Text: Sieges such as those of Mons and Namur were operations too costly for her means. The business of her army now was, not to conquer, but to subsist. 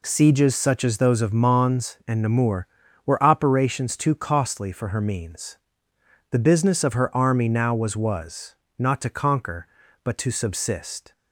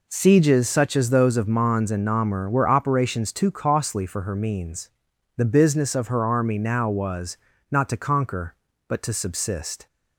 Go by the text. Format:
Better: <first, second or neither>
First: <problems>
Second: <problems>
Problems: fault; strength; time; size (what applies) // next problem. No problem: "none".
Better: second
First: says "was" twice; at 7.9 s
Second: none